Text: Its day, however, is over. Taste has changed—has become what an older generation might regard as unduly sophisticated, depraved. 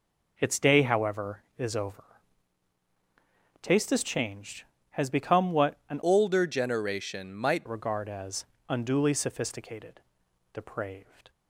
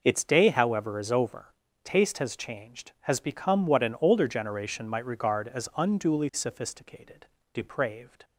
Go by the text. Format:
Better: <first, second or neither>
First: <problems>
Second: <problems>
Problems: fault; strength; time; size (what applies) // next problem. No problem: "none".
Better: second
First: changes voice from "older" to "might"; from 6.0 to 7.6 s; 1.6 s long // pauses between "as" and "unduly"; slight; at 8.4 s; 0.24 s long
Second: none